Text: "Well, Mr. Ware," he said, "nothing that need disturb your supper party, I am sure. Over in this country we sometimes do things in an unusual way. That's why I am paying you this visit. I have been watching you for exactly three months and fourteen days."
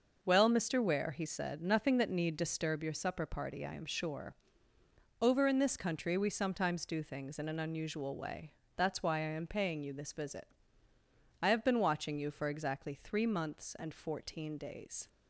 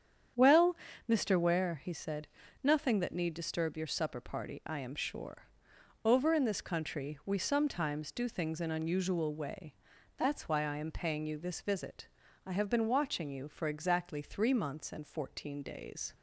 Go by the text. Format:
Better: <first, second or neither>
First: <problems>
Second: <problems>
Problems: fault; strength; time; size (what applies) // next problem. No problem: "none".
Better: first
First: starts louder than the rest; noticeable; until 1.2 s; 6 dB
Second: starts louder than the rest; strong; until 1.6 s; 8.5 dB // skips "an"; at 8.6 s